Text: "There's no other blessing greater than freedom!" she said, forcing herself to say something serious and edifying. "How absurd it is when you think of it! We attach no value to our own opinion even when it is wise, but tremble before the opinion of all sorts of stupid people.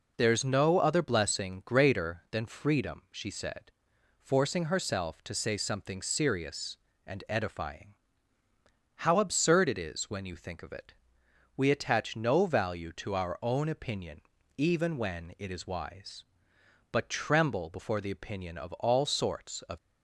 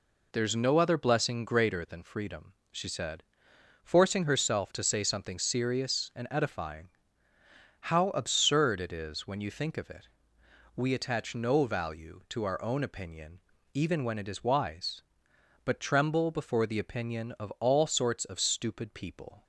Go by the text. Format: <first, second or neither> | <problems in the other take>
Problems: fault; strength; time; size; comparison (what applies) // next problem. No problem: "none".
second | pauses between "opinion" and "even"; slight; at 14.2 s; 0.34 s long; slight in the second // stops before "stupid people"; at 19.7 s